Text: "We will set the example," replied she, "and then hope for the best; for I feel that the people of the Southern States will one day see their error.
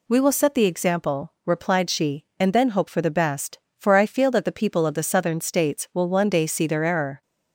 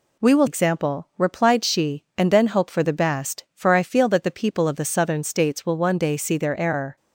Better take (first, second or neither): first